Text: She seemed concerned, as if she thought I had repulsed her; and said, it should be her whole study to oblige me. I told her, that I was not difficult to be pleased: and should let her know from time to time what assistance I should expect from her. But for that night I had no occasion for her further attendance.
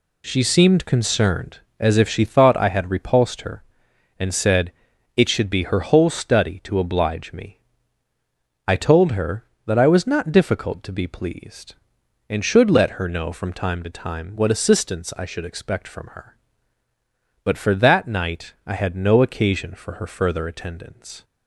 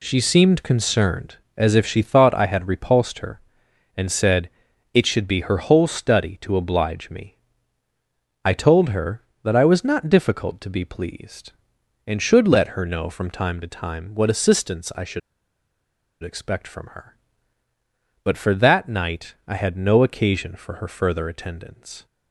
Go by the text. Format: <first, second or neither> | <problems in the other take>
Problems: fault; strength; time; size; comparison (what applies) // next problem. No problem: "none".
first | pauses between "should" and "expect"; at 15.1 s; 1.0 s long